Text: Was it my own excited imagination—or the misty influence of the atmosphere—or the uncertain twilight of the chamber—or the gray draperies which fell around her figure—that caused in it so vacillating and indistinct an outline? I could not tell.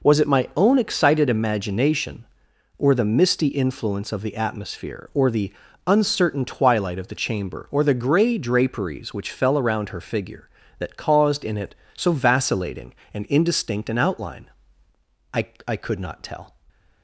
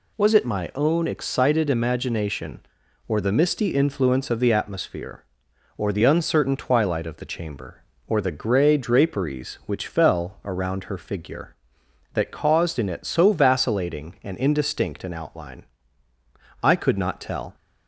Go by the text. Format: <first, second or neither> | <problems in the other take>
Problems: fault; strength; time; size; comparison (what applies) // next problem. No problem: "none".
second | pauses between "the" and "uncertain"; slight; at 5.5 s; 0.34 s long // says "I" twice; at 15.6 s